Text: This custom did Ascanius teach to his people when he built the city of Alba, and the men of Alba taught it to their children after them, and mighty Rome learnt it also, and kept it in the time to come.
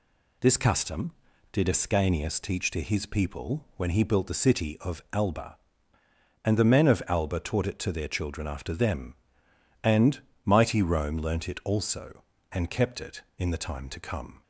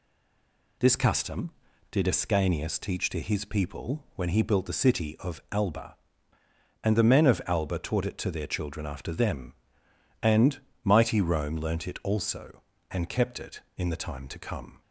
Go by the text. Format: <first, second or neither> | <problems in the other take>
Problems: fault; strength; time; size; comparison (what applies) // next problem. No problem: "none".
first | stays silent before the first word; slight; until 0.7 s; 0.7 s long // pauses between "and" and "mighty"; slight; at 10.5 s; 0.24 s long; slight in the first